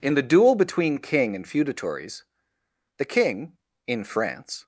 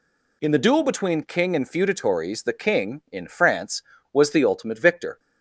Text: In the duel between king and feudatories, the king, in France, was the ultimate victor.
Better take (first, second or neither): second